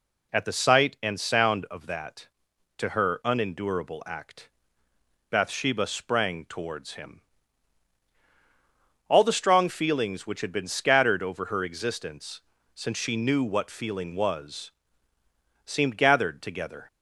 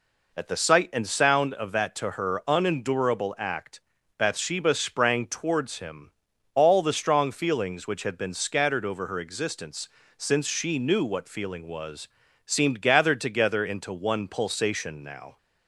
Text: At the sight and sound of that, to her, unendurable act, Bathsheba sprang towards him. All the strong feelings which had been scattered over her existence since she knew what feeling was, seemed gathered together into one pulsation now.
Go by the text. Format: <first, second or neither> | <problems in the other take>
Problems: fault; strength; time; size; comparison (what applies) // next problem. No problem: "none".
second | pauses between "existence" and "since"; slight; at 12.4 s; 0.32 s long; slight in the second // stops before "into one pulsation now"; at 16.8 s